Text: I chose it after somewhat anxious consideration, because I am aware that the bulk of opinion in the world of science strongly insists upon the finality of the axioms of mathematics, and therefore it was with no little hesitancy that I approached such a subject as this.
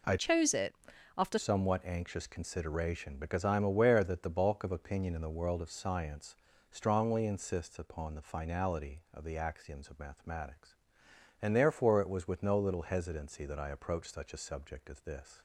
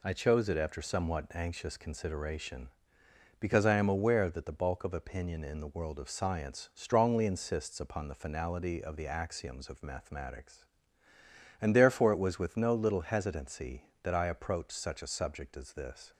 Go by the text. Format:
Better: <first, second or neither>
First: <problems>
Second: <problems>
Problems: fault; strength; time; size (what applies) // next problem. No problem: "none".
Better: second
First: changes voice from "chose" to "after"; from 0.1 to 1.3 s; 1.2 s long // pauses between "it" and "after"; at 0.7 s; 0.42 s long // pauses between "science" and "strongly"; slight; at 6.3 s; 0.36 s long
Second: none